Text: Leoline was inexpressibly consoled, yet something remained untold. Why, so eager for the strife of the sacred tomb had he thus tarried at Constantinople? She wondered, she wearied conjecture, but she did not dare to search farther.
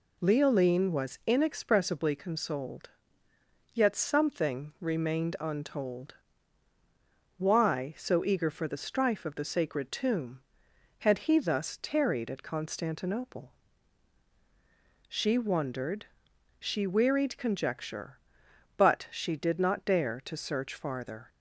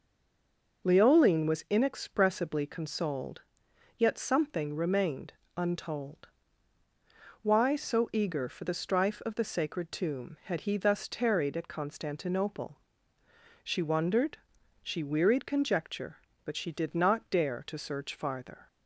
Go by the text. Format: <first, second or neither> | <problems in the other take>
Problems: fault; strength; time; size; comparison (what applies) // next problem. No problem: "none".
first | stays silent before the first word; slight; until 0.8 s; 0.8 s long // pauses between "remained" and "untold"; slight; at 5.3 s; 0.24 s long